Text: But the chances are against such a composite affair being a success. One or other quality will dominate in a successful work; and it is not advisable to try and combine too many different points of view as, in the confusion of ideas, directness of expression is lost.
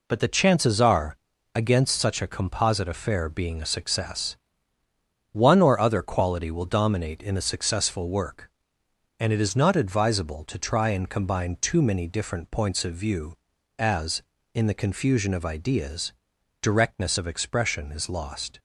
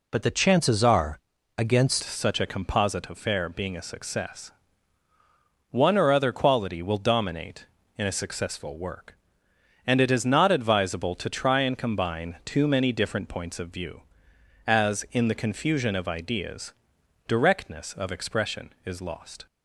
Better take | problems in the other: first | pauses between "are" and "against"; at 1.1 s; 0.38 s long; also in the first // changes voice at "such"; from 2.0 s on; 17.4 s long

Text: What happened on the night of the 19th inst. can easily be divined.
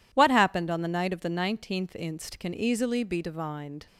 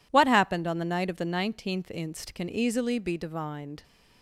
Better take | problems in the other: neither | none

